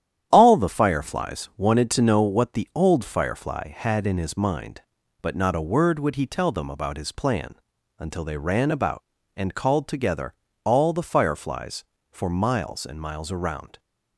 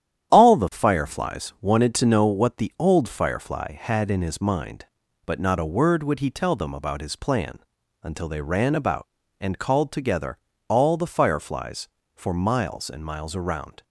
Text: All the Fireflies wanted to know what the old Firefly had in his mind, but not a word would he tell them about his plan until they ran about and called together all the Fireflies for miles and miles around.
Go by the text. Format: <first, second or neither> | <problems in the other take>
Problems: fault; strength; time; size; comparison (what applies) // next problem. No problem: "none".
neither | starts louder than the rest; strong; the same in both // pauses between "plan" and "until"; the same in both // pauses between "together" and "all"; slight; the same in both